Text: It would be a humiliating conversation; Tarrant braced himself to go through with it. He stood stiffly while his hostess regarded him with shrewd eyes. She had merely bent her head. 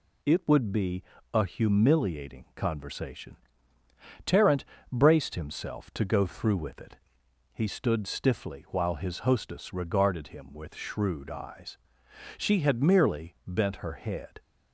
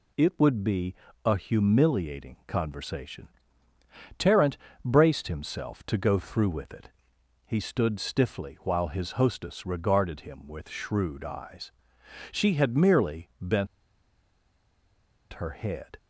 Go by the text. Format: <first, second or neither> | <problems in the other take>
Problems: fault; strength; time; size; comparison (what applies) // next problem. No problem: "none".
first | pauses between "be" and "a"; slight; at 0.9 s; 0.32 s long; slight in the first // pauses between "Tarrant" and "braced"; slight; at 4.5 s; 0.28 s long; slight in the first // pauses between "bent" and "her"; strong; at 13.6 s; 1.6 s long